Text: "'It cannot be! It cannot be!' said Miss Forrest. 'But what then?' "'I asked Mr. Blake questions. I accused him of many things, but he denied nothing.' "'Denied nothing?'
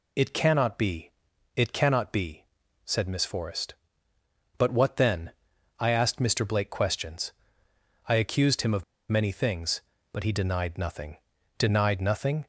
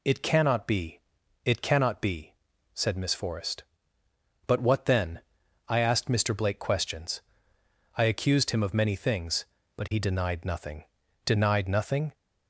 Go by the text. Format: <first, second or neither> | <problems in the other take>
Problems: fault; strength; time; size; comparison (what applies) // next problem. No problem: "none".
second | pauses between "of" and "many"; slight; at 8.8 s; 0.25 s long